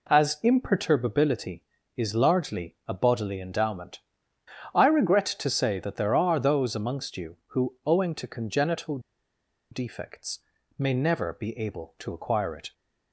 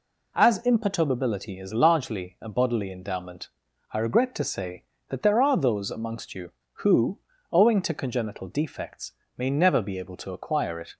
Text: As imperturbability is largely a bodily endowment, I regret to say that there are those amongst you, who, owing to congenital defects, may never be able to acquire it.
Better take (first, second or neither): second